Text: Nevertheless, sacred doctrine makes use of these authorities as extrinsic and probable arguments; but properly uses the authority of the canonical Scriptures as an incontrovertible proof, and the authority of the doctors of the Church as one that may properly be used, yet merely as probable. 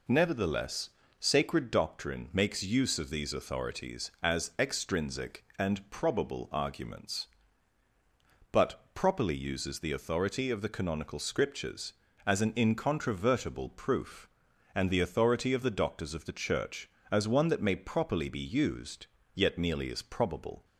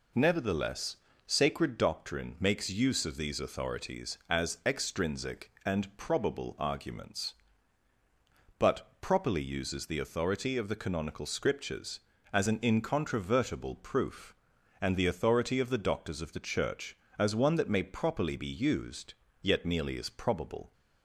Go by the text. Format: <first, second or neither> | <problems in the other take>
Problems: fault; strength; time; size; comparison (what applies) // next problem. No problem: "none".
neither | none